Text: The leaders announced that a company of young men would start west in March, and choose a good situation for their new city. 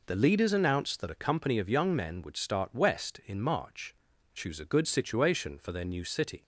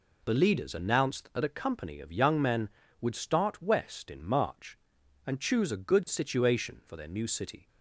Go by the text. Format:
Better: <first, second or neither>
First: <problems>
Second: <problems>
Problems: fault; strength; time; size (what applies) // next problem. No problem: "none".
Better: second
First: skips "and"; at 4.1 s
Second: none